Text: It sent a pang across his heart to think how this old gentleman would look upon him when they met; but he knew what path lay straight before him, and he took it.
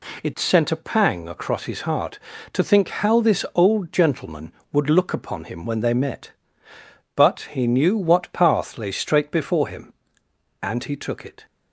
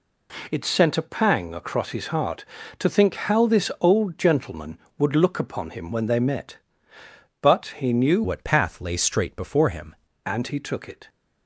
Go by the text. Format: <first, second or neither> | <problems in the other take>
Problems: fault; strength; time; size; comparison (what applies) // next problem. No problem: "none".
first | changes voice from "what" to "him"; from 8.2 to 9.9 s; 1.7 s long